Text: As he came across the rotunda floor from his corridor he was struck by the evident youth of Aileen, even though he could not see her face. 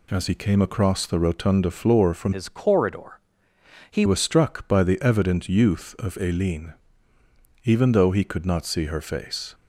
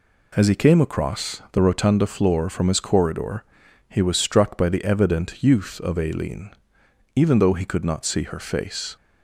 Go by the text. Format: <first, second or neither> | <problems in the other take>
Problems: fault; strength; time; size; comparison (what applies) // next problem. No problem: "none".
second | changes voice from "his" to "he"; from 2.3 to 4.0 s; 1.7 s long // pauses between "corridor" and "he"; noticeable; at 3.1 s; 0.70 s long; also in the second